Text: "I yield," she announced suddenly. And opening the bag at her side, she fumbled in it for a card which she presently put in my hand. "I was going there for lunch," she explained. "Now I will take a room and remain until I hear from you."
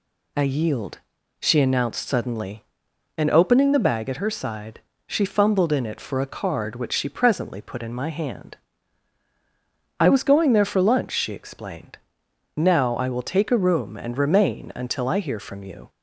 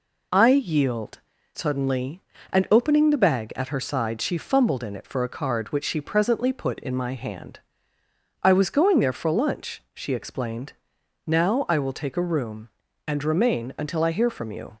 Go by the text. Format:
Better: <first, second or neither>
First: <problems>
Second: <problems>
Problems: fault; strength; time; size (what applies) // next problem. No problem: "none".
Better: first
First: none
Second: skips "she announced"; at 1.3 s